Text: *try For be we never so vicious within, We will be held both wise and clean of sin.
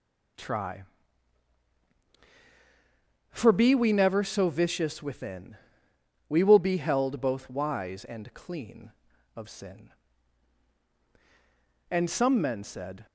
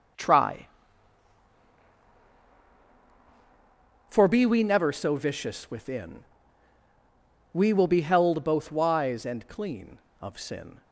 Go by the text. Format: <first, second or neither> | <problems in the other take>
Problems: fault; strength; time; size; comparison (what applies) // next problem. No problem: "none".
second | goes on to say "And some men said"; noticeable; from 11.9 s on; 1.1 s long